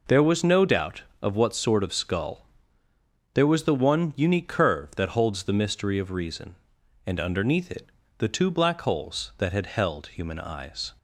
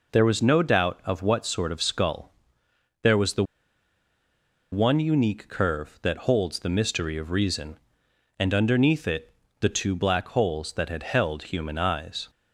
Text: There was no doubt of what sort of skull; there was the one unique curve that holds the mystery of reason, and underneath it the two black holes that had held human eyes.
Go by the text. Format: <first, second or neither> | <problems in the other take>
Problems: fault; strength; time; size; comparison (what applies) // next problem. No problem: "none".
first | pauses between "the" and "one"; strong; at 3.4 s; 1.2 s long // pauses between "it" and "the"; slight; at 9.3 s; 0.26 s long; slight in the first